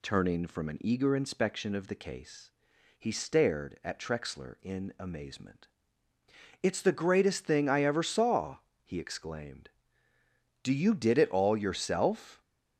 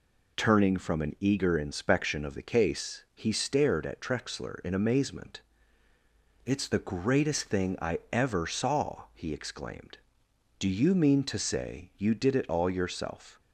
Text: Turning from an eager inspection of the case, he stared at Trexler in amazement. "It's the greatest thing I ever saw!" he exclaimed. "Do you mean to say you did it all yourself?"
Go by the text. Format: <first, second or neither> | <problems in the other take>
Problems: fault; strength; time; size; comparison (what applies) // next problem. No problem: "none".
second | skips "you mean to say"; at 10.7 s